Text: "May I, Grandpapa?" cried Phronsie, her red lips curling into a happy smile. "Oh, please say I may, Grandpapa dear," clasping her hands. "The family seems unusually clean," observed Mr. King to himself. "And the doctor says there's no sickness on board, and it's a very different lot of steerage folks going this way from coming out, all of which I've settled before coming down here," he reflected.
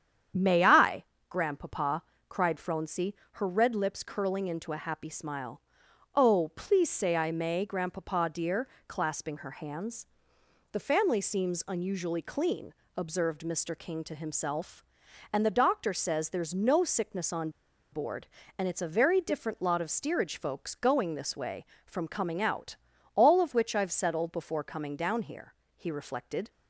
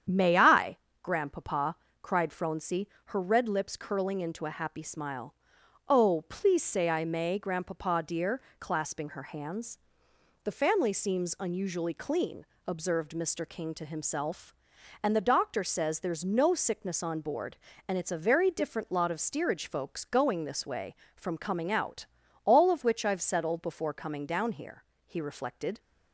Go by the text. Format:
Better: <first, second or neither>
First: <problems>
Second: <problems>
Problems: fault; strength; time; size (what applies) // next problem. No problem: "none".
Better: second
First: starts louder than the rest; strong; until 1.6 s; 8.5 dB // pauses between "on" and "board"; at 17.4 s; 0.43 s long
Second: starts louder than the rest; strong; until 1.3 s; 8.5 dB